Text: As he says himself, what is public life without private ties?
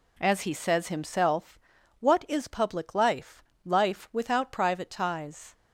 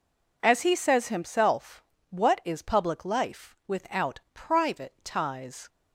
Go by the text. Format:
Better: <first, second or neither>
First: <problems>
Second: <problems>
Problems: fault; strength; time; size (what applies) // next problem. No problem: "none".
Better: second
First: says "life" twice; at 3.6 s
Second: none